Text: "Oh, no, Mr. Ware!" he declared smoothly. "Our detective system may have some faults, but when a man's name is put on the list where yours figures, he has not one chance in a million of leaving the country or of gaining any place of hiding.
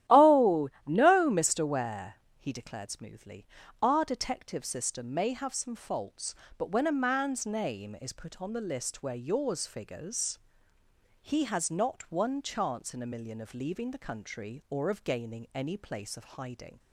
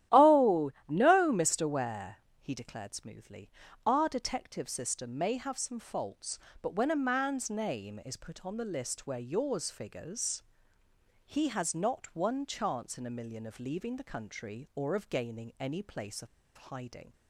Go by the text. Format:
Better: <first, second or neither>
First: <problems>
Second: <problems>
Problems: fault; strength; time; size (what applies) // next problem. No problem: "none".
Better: first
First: starts louder than the rest; strong; until 1.2 s; 12.5 dB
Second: starts louder than the rest; strong; until 1.2 s; 12.5 dB // pauses between "of" and "hiding"; slight; at 16.2 s; 0.28 s long